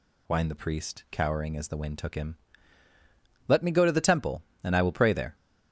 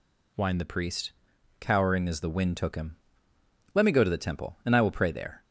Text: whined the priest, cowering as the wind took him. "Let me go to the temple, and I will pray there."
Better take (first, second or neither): neither